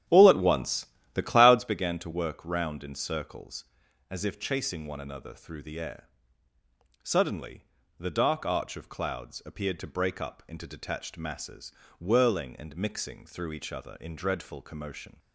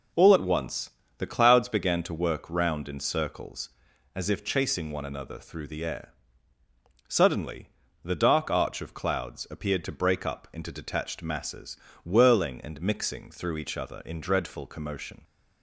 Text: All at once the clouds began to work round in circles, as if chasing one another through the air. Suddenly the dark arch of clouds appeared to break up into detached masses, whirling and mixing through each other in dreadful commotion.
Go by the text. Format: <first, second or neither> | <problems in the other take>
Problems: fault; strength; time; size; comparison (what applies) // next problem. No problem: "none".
second | starts louder than the rest; strong; until 1.7 s; 10 dB // pauses between "once" and "the"; slight; at 0.8 s; 0.28 s long; slight in the second // pauses between "Suddenly" and "the"; slight; at 7.6 s; 0.34 s long; slight in the second